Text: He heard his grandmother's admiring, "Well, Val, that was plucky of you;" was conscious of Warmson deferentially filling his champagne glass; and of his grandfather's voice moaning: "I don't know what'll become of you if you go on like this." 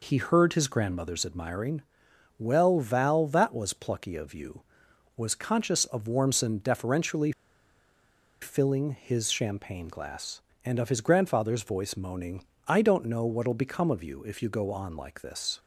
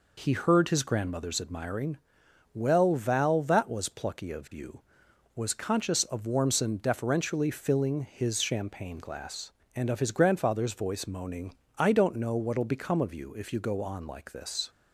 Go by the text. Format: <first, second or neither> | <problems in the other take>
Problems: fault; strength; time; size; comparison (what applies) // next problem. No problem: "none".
second | pauses between "deferentially" and "filling"; at 7.3 s; 1.1 s long